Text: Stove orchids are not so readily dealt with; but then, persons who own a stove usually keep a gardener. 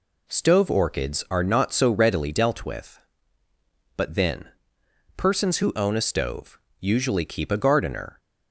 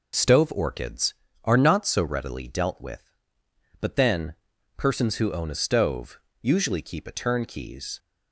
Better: first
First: pauses between "stove" and "usually"; slight; at 6.5 s; 0.22 s long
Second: pauses between "stove" and "usually"; slight; at 6.2 s; 0.20 s long // says "turnkeys" for "gardener"; at 7.1 s

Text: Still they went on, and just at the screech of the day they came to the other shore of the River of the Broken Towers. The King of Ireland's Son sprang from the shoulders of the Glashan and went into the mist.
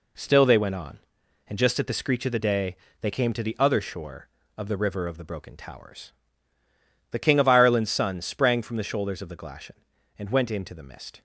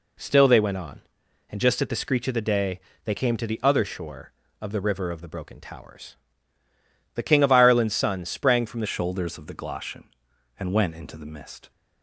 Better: first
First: pauses between "day" and "they"; slight; at 2.7 s; 0.24 s long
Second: pauses between "day" and "they"; slight; at 2.8 s; 0.24 s long // changes voice at "shoulders"; from 8.8 s on; 2.9 s long

